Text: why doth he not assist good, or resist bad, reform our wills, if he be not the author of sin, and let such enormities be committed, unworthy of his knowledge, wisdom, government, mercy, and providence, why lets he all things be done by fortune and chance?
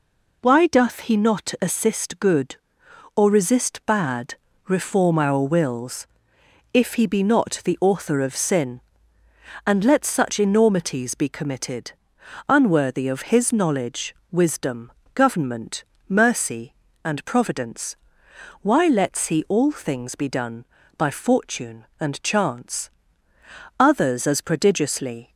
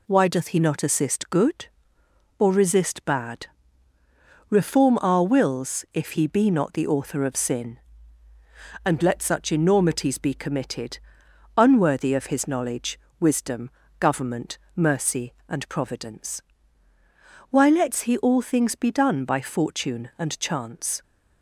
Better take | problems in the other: second | goes on to say "Others as prodigiously"; from 23.7 s on; 1.5 s long

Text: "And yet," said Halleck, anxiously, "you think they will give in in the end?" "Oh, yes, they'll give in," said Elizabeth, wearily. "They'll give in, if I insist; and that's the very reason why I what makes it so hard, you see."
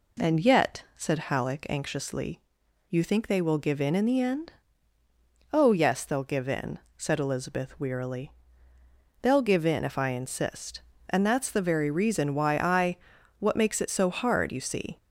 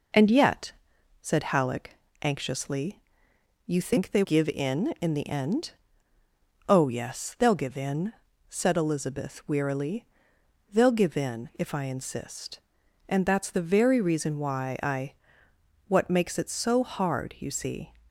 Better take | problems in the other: first | skips "will"; at 4.2 s // pauses between "I" and "what"; noticeable; at 15.1 s; 0.74 s long; also in the first

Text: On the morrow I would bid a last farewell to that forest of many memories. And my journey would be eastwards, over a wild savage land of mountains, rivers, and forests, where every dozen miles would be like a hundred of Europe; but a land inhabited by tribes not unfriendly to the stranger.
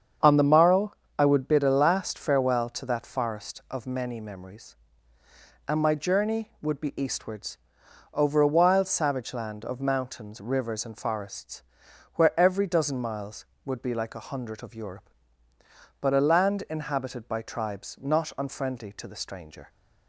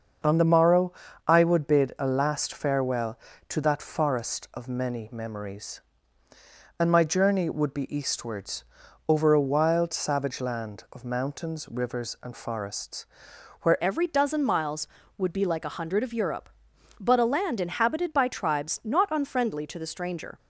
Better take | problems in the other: first | starts louder than the rest; until 1.5 s; 6.5 dB; strong in the first // pauses between "morrow" and "I"; slight; at 0.9 s; 0.34 s long; slight in the first // changes voice at "every"; from 13.8 s on; 6.5 s long

